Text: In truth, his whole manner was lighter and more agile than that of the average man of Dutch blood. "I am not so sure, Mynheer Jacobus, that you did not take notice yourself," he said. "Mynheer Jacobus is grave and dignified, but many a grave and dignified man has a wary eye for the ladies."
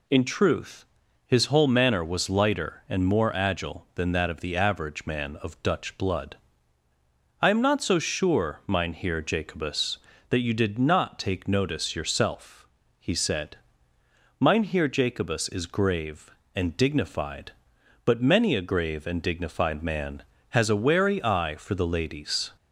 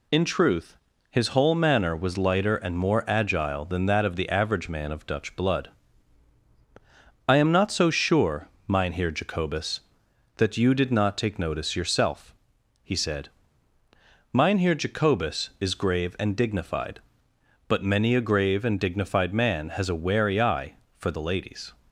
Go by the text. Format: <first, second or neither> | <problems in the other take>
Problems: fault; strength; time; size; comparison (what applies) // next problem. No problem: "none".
neither | none